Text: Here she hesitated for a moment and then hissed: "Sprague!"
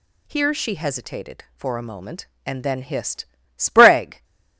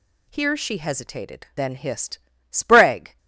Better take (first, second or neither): first